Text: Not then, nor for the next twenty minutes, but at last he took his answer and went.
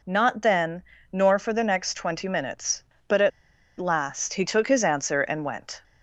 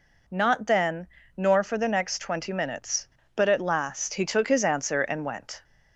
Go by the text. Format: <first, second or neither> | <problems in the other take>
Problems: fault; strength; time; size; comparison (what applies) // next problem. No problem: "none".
second | pauses between "at" and "last"; noticeable; at 3.3 s; 0.48 s long